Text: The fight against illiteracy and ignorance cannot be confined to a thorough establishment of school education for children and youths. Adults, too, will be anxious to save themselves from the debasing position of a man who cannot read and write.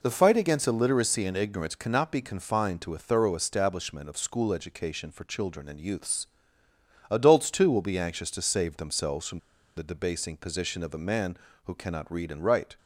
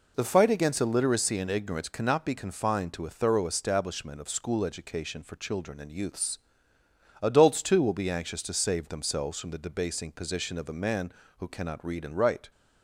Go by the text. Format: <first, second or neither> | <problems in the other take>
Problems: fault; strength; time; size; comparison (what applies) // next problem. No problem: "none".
second | pauses between "from" and "the"; at 9.3 s; 0.38 s long